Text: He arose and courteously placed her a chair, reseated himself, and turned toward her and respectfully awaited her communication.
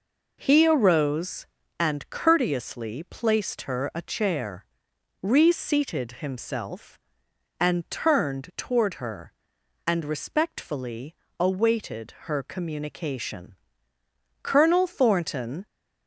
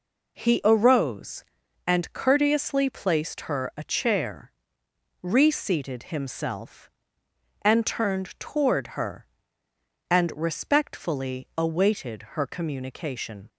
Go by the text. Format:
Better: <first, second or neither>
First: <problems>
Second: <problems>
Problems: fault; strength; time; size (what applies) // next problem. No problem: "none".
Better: second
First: pauses between "respectfully" and "awaited"; slight; at 11.1 s; 0.28 s long // goes on to say "Colonel Thornton"; noticeable; from 14.4 s on; 1.2 s long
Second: none